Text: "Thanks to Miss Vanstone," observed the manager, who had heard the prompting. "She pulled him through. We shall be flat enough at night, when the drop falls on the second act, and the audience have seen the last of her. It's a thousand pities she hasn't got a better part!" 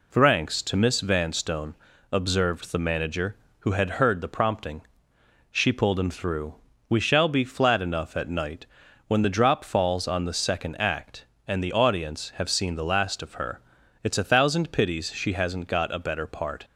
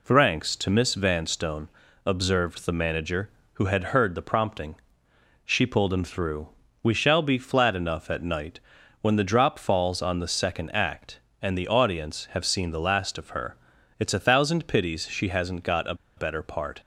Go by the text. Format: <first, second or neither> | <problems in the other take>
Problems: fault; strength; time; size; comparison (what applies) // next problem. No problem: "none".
first | pauses between "a" and "better"; slight; at 15.9 s; 0.22 s long